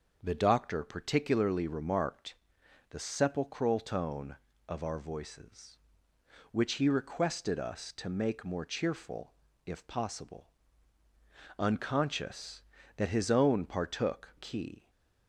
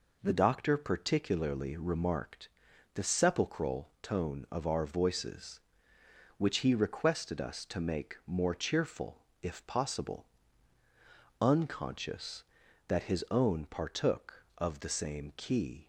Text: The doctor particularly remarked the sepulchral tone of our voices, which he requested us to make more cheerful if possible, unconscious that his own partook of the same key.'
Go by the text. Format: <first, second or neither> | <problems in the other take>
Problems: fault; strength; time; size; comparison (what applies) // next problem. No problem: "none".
second | starts louder than the rest; until 1.2 s; 6.5 dB // pauses between "remarked" and "the"; noticeable; at 2.3 s; 0.56 s long; noticeable in the second // pauses between "cheerful" and "if"; slight; at 9.3 s; 0.32 s long; slight in the second // skips "of the same"; at 14.3 s